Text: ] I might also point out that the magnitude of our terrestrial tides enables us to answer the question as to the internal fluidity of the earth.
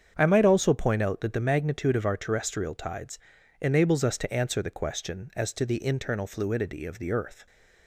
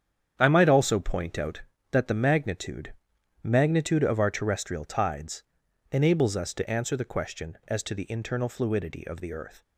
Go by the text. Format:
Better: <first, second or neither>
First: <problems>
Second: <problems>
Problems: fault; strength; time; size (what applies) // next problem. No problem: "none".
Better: first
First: starts louder than the rest; strong; until 1.1 s; 7.5 dB // pauses between "tides" and "enables"; at 3.1 s; 0.42 s long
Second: starts louder than the rest; strong; until 1.3 s; 8.5 dB // says "magnitude" twice; at 3.4 s // pauses between "tides" and "enables"; noticeable; at 5.4 s; 0.48 s long